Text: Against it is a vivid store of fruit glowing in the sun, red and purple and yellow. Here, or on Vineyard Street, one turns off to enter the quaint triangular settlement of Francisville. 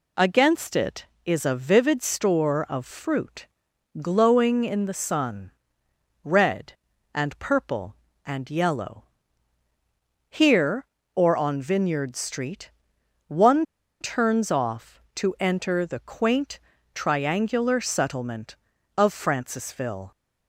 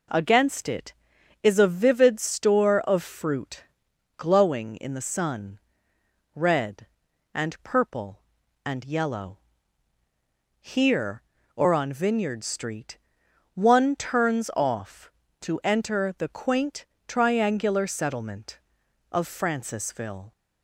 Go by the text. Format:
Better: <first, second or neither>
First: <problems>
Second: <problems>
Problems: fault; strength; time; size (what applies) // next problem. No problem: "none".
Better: second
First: pauses between "fruit" and "glowing"; noticeable; at 3.4 s; 0.54 s long // pauses between "one" and "turns"; at 13.6 s; 0.36 s long // pauses between "quaint" and "triangular"; slight; at 16.6 s; 0.32 s long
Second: pauses between "fruit" and "glowing"; noticeable; at 3.6 s; 0.50 s long // pauses between "quaint" and "triangular"; slight; at 16.8 s; 0.22 s long